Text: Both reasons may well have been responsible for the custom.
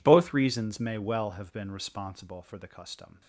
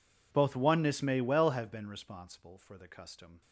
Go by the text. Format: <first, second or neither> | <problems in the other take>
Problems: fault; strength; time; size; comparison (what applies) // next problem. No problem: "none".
first | says "oneness" for "reasons"; at 0.5 s